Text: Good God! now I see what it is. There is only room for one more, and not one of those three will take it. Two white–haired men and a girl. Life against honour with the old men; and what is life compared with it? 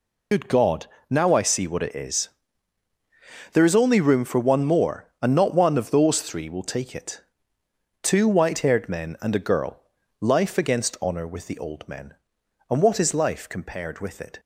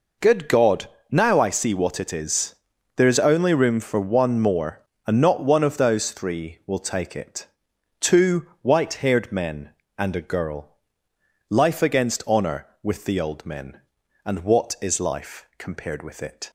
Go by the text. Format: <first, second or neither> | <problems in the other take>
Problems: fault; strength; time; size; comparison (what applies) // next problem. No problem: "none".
second | loses the start of "Good"; at 0.3 s; 55 ms